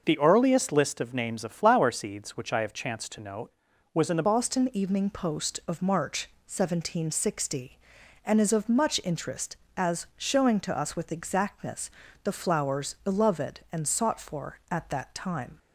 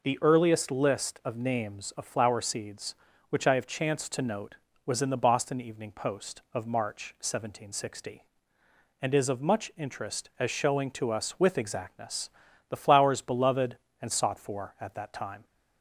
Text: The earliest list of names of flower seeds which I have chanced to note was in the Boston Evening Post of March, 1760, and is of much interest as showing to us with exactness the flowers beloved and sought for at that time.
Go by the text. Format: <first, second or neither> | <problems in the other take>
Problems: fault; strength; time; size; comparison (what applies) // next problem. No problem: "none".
second | starts louder than the rest; noticeable; until 1.0 s; 6 dB // changes voice at "Boston"; from 4.2 s on; 11.3 s long // pauses between "exactness" and "the"; slight; at 11.8 s; 0.32 s long; also in the second